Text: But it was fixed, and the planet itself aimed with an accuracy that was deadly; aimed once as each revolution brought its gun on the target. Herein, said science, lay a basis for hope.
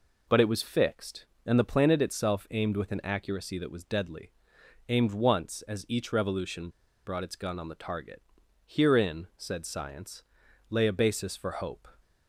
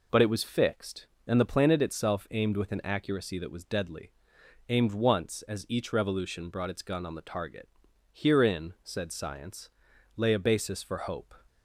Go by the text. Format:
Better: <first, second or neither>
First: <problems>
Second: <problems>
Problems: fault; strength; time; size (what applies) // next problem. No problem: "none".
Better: second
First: pauses between "revolution" and "brought"; at 6.6 s; 0.36 s long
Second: none